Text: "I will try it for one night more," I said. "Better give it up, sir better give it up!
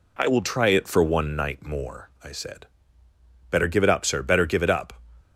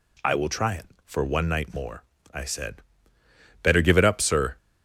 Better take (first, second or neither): first